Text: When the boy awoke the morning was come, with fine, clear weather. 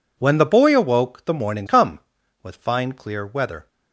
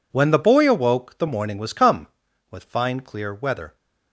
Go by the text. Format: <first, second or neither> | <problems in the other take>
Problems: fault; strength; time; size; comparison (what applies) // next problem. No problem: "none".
second | skips "was"; at 1.6 s